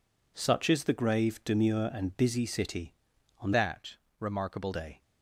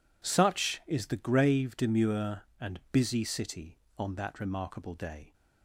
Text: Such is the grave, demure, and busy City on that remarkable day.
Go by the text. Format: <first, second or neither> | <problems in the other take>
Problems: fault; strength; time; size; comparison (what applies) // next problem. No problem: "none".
second | changes voice from "that" to "remarkable"; from 3.5 to 4.7 s; 1.2 s long // pauses between "that" and "remarkable"; slight; at 3.9 s; 0.22 s long